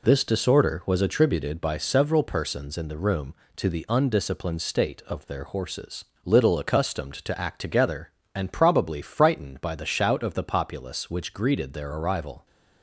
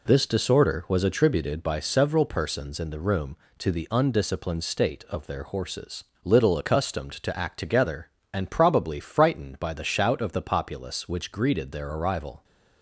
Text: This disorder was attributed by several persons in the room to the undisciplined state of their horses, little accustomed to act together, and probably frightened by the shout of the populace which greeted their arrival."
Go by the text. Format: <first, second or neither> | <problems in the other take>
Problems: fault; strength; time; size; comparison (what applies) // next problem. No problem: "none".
neither | none